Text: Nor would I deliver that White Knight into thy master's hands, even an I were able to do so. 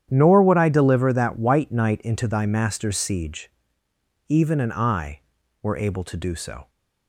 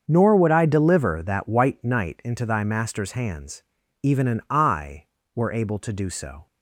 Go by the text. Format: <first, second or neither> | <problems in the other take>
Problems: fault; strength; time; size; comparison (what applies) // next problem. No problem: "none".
second | starts louder than the rest; strong; until 1.1 s; 9.5 dB; also in the second // says "siege" for "hands"; at 2.9 s